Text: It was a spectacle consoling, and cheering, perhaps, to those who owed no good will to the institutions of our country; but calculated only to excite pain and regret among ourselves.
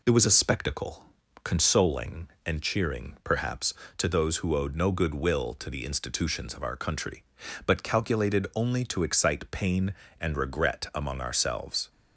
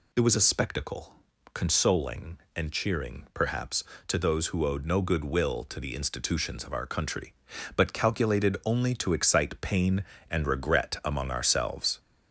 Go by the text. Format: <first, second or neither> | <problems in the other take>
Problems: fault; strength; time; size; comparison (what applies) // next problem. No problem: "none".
first | gets louder; slight; throughout; 3 dB // pauses between "spectacle" and "consoling"; at 1.1 s; 0.40 s long; also in the first